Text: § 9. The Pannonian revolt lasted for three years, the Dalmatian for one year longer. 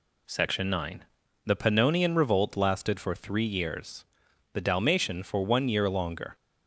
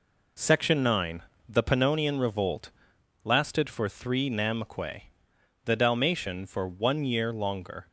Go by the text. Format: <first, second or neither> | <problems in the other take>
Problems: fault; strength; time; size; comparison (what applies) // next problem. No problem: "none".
first | pauses between "revolt" and "lasted"; noticeable; at 2.6 s; 0.54 s long // says "namque" for "years"; at 4.2 s